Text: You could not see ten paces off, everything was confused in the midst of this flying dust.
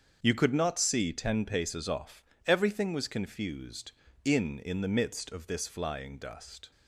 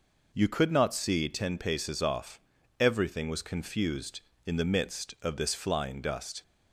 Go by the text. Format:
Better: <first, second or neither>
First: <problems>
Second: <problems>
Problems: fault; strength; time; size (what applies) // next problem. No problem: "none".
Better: second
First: starts louder than the rest; strong; until 1.2 s; 7 dB // says "in" twice; at 4.5 s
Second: none